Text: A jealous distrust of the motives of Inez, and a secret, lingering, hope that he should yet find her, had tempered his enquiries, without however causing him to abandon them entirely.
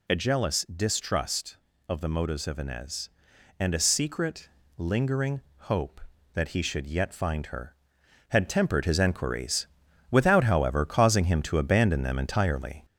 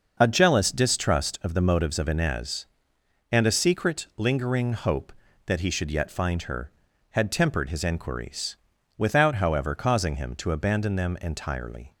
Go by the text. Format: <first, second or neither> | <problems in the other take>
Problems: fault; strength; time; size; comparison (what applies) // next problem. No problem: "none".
second | gets louder; slight; throughout; 2.5 dB